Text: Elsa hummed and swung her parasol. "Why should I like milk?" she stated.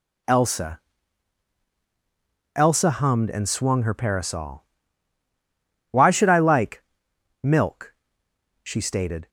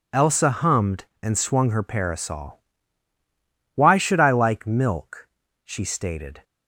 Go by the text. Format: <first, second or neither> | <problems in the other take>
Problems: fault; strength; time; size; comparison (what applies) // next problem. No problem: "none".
second | says "Elsa" twice; at 2.5 s // pauses between "like" and "milk"; noticeable; at 6.8 s; 0.60 s long